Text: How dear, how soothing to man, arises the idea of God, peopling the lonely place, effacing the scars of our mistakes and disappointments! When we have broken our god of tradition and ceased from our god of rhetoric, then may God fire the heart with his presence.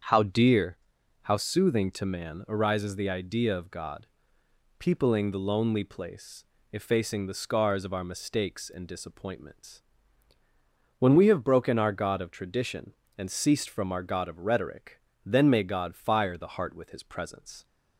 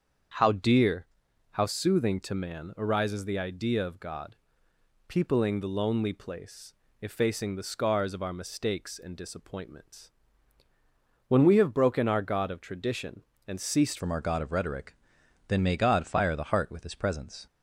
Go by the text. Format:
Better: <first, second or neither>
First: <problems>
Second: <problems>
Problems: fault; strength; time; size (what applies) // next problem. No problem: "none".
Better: first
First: starts louder than the rest; strong; until 1.5 s; 7.5 dB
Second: starts louder than the rest; strong; until 1.8 s; 7.5 dB // changes voice at "from"; from 13.9 s on; 3.5 s long